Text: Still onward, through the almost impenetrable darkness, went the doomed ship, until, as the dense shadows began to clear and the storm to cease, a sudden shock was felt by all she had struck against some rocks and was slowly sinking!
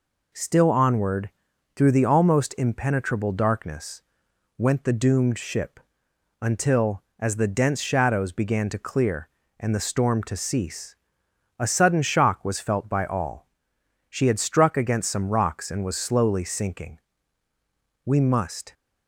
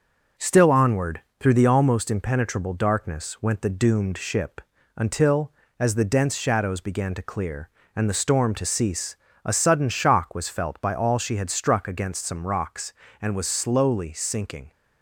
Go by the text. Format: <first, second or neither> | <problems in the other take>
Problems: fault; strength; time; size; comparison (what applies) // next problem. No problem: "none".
second | pauses between "all" and "she"; noticeable; at 13.4 s; 0.62 s long // goes on to say "We must"; noticeable; from 18.0 s on; 0.68 s long